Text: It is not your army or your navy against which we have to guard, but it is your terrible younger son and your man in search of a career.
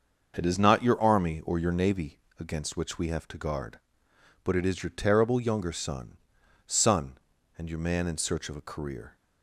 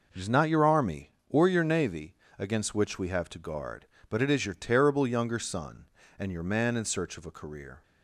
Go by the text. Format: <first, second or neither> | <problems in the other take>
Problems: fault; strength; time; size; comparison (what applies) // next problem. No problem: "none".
second | starts louder than the rest; until 1.3 s; 6.5 dB // pauses between "navy" and "against"; slight; at 2.1 s; 0.20 s long; slight in the second // says "son" twice; at 6.6 s